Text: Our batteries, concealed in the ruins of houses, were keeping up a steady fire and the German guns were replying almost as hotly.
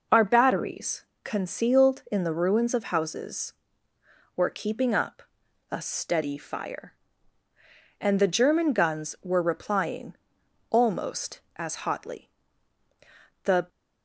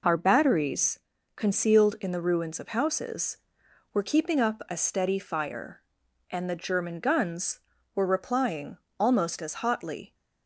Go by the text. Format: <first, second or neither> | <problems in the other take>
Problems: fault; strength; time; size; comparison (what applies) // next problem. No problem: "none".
second | pauses between "up" and "a"; noticeable; at 5.2 s; 0.48 s long // pauses between "replying" and "almost"; noticeable; at 10.1 s; 0.88 s long; slight in the second // goes on to say "The"; slight; from 13.4 s on; 0.26 s long